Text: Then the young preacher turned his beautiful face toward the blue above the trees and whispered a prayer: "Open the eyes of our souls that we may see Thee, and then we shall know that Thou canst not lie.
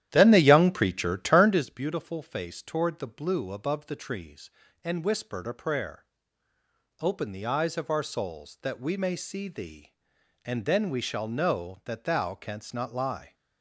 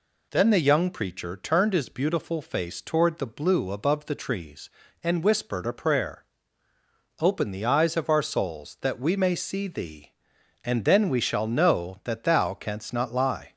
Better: second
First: starts louder than the rest; strong; until 1.7 s; 11.5 dB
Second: none

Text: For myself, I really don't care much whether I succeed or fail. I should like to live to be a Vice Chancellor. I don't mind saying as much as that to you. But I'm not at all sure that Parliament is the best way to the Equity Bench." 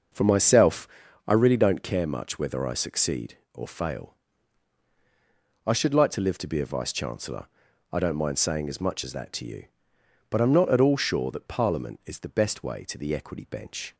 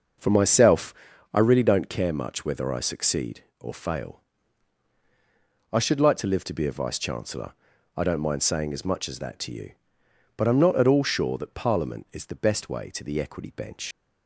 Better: first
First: none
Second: leaves "Bench" unfinished; at 13.9 s; 95 ms

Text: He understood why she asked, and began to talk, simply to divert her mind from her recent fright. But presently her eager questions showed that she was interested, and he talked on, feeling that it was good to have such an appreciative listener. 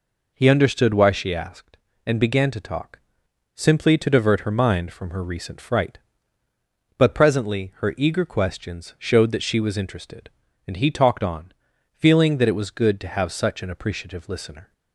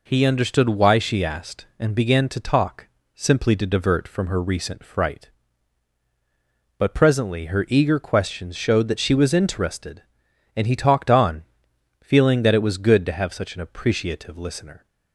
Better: first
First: none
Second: skips "her mind"; at 4.0 s

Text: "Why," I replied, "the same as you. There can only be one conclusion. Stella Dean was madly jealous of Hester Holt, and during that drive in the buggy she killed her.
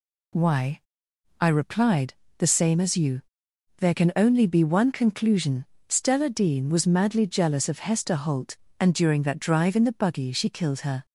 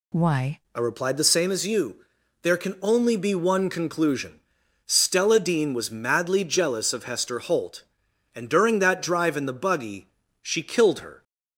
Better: first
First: none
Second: changes voice at "I"; from 0.7 s on; 10.5 s long // pauses between "buggy" and "she"; slight; at 10.0 s; 0.32 s long

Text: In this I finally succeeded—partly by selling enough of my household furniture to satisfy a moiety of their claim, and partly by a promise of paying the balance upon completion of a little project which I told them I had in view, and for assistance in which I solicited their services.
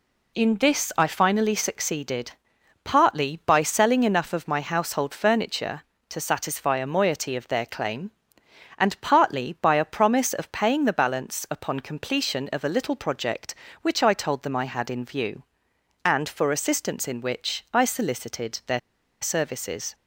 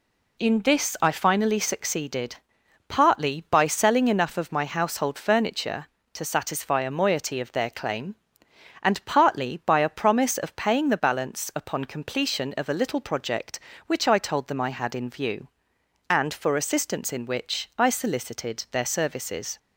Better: second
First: pauses between "their" and "services"; at 18.7 s; 0.42 s long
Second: none

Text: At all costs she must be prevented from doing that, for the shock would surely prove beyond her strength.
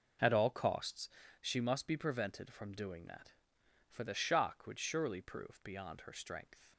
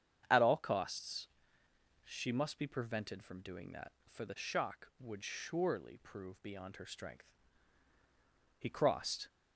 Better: first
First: pauses between "costs" and "she"; slight; at 1.0 s; 0.32 s long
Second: starts louder than the rest; strong; until 2.0 s; 8 dB // pauses between "costs" and "she"; noticeable; at 1.2 s; 0.78 s long // goes on to say "He crossed"; noticeable; from 8.5 s on; 0.70 s long

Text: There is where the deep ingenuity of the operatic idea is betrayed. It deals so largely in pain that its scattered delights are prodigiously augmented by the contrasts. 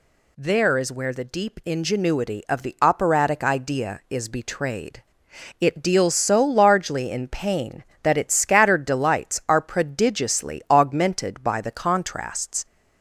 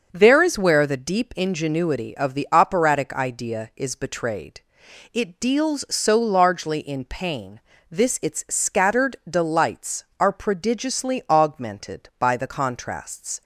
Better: first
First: none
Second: starts louder than the rest; until 1.1 s; 6.5 dB // says "this" for "that"; at 7.9 s

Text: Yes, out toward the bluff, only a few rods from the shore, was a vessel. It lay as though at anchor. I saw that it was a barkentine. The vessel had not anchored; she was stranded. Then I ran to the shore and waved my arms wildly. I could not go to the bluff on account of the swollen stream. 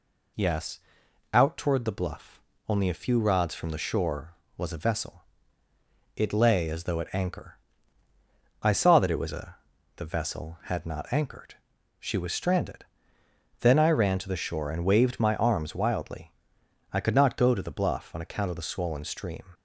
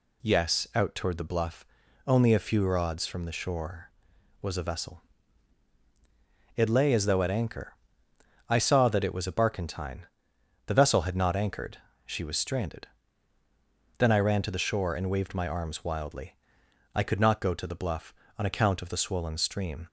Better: second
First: skips "barkentine"; at 9.7 s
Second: none

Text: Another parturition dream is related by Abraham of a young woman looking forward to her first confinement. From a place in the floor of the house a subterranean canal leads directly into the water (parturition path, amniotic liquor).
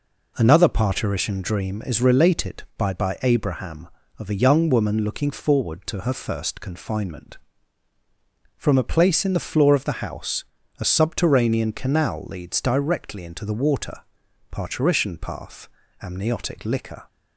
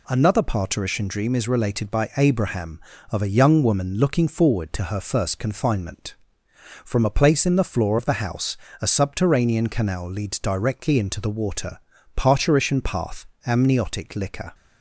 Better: second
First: says "by" twice; at 2.9 s // pauses between "house" and "a"; slight; at 10.4 s; 0.36 s long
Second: pauses between "house" and "a"; slight; at 8.5 s; 0.22 s long

